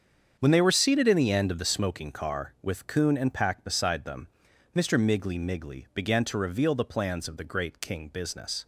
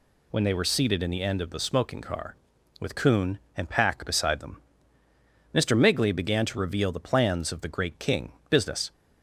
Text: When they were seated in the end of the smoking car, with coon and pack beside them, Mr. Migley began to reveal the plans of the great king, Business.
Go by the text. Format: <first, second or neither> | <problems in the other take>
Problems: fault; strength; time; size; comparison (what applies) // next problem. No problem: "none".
second | starts louder than the rest; strong; until 1.4 s; 7.5 dB // says "Migley" twice; at 5.3 s